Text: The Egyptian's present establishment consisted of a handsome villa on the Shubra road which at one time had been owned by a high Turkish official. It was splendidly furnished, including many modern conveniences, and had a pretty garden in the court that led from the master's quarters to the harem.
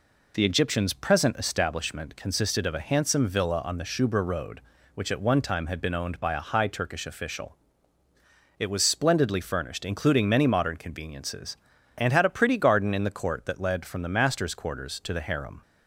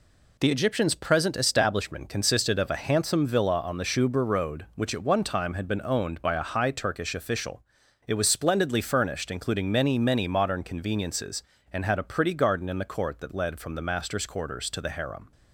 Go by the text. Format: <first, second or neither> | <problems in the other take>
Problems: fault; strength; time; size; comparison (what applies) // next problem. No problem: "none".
first | says "many" twice; at 9.9 s